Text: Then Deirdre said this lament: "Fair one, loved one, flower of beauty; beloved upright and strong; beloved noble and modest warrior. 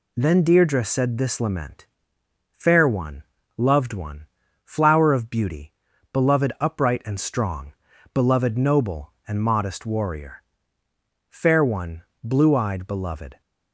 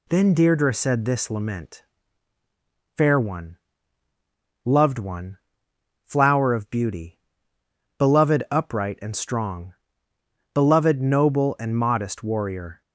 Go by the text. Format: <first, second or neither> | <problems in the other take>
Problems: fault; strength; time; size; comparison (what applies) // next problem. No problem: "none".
second | goes on to say "Fair one blue eyed beloved"; strong; from 11.2 s on; 2.1 s long